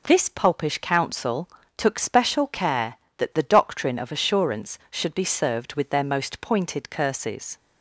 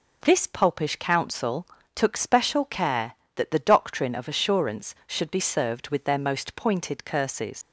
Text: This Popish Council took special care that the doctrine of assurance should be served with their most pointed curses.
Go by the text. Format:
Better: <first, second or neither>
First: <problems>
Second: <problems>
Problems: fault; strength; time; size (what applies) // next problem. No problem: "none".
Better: first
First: pauses between "Council" and "took"; slight; at 1.4 s; 0.28 s long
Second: pauses between "Council" and "took"; slight; at 1.6 s; 0.28 s long // leaves "curses" unfinished; at 7.6 s; 100 ms